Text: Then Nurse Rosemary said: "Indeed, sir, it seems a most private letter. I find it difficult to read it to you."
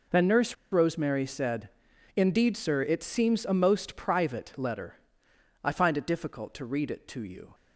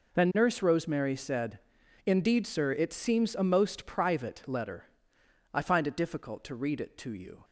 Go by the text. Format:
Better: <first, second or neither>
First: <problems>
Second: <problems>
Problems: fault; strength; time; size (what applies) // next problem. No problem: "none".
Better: second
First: pauses between "Nurse" and "Rosemary"; slight; at 0.5 s; 0.17 s long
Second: none